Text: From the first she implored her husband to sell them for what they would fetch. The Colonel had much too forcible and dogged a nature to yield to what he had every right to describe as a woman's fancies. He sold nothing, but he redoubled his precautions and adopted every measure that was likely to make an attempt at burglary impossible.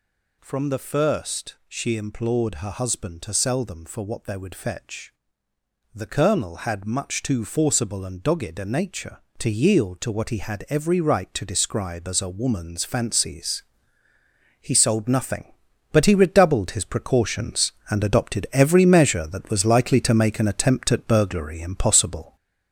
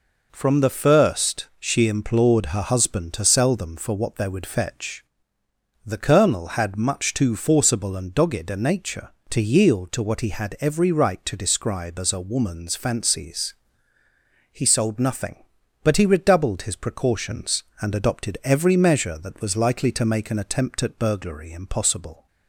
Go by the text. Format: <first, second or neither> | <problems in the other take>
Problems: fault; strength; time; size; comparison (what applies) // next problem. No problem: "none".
second | gets louder; noticeable; throughout; 5.5 dB